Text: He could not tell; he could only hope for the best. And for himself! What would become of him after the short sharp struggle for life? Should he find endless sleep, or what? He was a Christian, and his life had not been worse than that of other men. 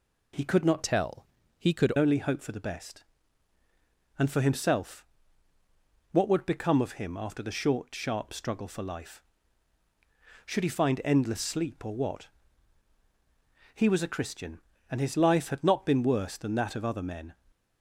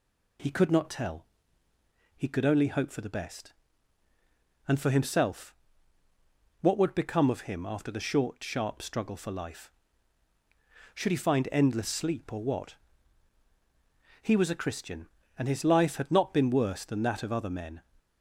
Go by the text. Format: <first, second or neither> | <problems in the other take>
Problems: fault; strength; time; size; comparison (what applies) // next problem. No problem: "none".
second | changes voice from "tell" to "could"; from 0.8 to 1.9 s; 1.1 s long